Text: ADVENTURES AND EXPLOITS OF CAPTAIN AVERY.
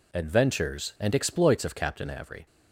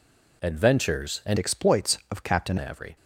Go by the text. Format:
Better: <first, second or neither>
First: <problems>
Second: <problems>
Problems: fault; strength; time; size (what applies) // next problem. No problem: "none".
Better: first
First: none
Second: changes voice from "EXPLOITS" to "CAPTAIN"; from 1.3 to 2.5 s; 1.2 s long